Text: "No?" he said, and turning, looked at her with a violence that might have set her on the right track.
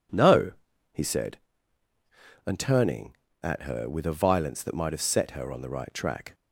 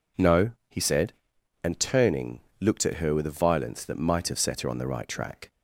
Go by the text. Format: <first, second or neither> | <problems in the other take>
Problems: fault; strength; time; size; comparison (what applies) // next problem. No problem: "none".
second | skips "looked"; at 3.3 s